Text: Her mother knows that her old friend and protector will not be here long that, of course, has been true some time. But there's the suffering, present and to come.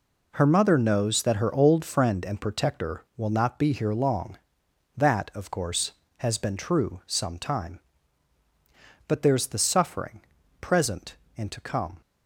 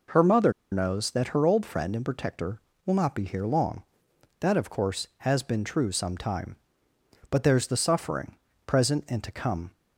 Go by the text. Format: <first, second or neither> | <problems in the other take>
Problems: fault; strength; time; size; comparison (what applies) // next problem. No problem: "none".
first | pauses between "mother" and "knows"; slight; at 0.5 s; 0.20 s long